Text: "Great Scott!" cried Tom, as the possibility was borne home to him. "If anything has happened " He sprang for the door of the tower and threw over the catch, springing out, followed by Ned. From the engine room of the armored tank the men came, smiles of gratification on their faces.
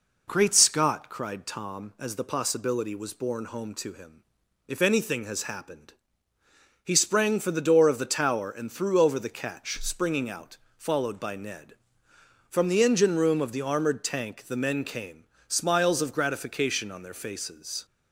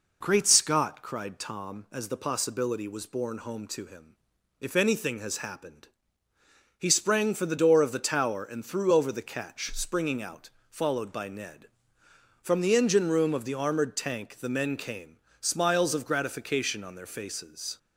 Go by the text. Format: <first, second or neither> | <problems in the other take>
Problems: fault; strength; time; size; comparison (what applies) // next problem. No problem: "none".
neither | none